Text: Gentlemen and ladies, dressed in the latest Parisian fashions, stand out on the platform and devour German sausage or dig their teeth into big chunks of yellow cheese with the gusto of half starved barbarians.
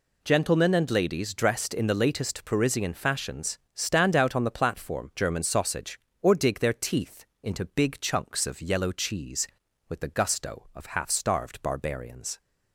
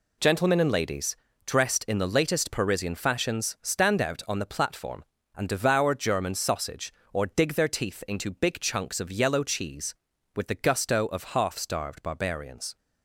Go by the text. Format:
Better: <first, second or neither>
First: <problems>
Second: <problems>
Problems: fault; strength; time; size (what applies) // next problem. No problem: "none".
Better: second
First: skips "and devour"; at 5.1 s // pauses between "teeth" and "into"; slight; at 7.2 s; 0.18 s long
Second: none